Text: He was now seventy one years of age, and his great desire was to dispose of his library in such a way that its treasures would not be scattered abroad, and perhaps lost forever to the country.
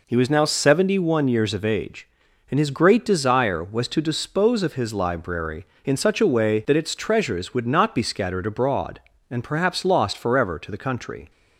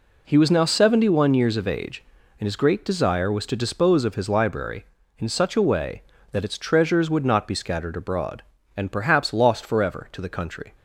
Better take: neither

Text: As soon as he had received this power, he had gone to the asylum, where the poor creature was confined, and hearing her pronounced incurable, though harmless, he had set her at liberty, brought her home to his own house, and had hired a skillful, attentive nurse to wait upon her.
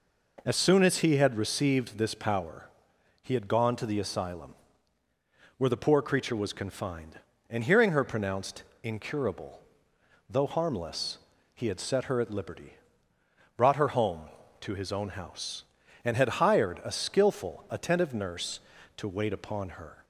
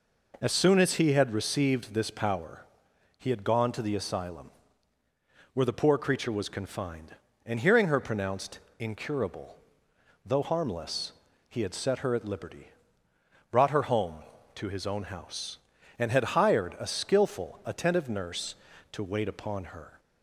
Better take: neither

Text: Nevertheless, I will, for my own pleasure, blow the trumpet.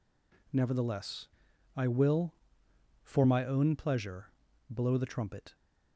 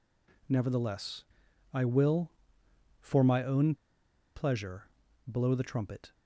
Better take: first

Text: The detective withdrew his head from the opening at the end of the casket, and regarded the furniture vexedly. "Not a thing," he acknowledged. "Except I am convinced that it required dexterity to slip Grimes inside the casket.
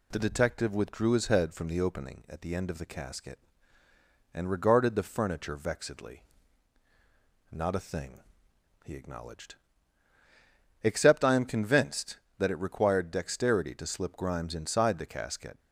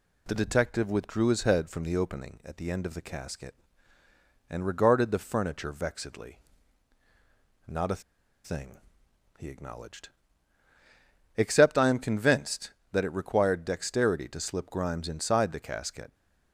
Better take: first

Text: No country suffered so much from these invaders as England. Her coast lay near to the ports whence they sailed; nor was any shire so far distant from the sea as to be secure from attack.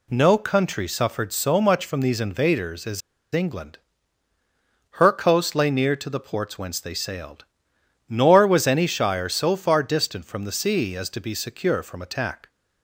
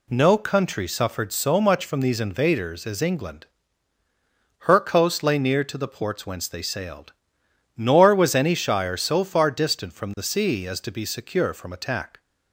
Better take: second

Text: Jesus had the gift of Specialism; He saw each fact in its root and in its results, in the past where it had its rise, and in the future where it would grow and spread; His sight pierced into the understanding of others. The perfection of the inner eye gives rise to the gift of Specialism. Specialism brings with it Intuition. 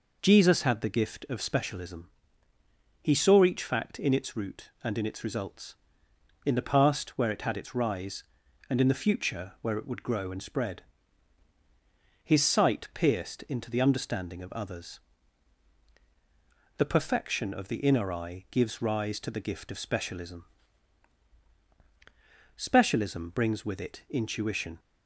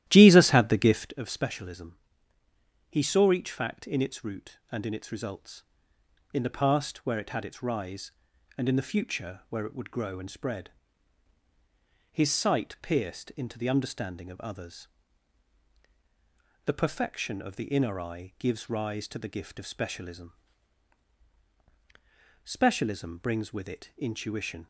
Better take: first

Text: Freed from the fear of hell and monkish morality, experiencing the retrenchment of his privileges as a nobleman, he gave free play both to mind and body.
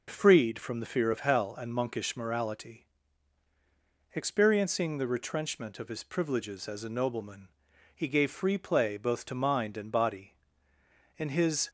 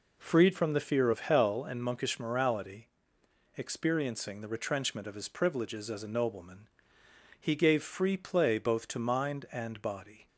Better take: second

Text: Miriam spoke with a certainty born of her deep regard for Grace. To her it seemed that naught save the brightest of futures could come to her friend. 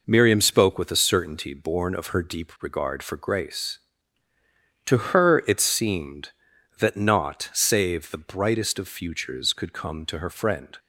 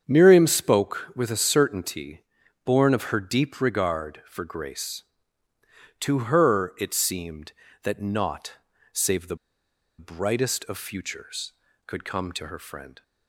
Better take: first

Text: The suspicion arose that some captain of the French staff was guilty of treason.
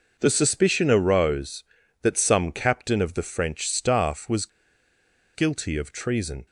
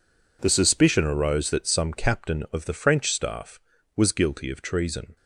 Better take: second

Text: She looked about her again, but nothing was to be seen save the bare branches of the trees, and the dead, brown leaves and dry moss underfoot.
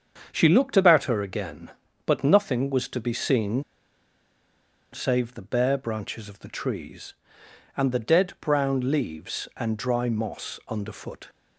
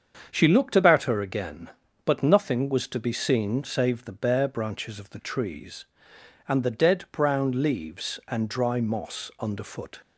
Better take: second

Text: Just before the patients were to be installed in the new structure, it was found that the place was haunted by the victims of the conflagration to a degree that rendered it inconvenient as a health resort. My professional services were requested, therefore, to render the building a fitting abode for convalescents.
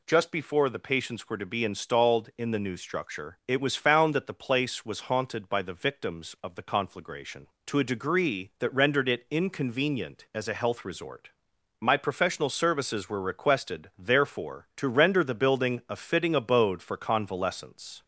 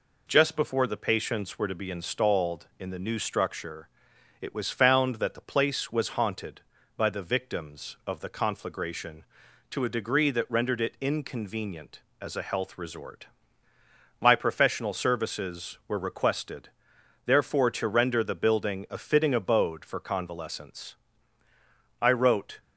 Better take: first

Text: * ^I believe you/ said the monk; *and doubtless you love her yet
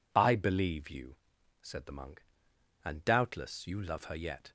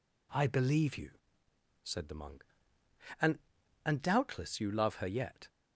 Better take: first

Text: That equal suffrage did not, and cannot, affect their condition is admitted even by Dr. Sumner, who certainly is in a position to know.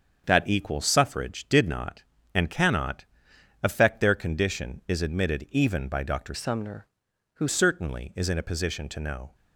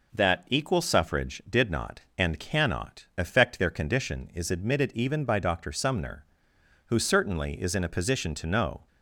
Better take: second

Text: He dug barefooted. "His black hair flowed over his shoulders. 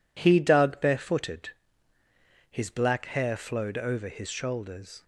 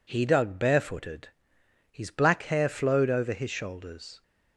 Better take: neither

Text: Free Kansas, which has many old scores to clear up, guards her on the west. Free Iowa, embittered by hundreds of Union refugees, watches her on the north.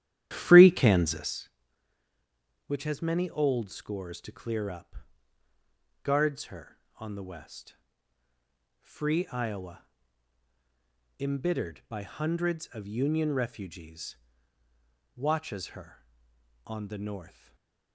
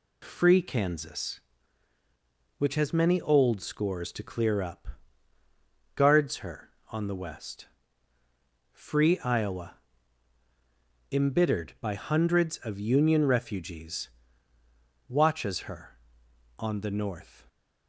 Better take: second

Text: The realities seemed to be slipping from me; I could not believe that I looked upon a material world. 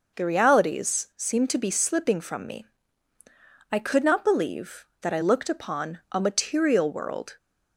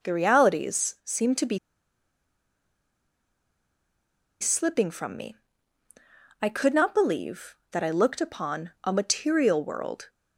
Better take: first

